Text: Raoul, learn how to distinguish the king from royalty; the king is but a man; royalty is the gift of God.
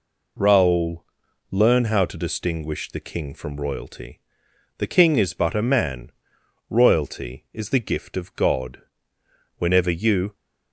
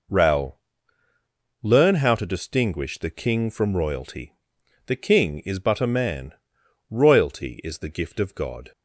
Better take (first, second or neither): second